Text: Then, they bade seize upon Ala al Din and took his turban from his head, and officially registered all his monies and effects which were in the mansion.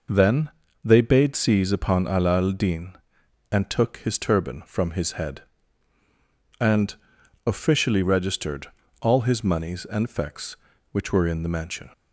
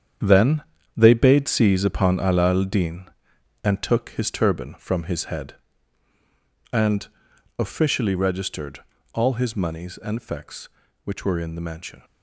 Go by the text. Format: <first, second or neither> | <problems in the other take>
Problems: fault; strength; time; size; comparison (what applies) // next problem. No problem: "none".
first | gets quieter; strong; throughout; 10 dB // pauses between "and" and "officially"; noticeable; at 7.0 s; 0.50 s long; noticeable in the first // pauses between "registered" and "all"; slight; at 8.7 s; 0.34 s long; slight in the first